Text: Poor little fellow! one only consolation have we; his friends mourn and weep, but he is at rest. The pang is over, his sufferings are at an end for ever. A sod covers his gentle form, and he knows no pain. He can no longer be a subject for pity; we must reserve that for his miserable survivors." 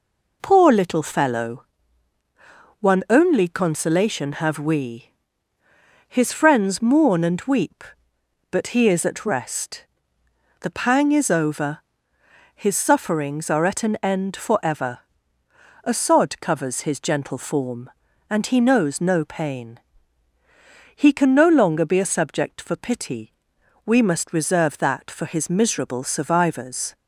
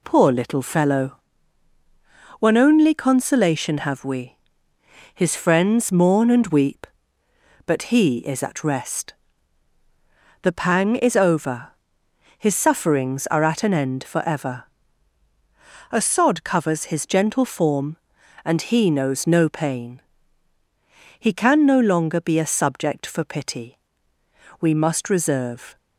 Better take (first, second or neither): first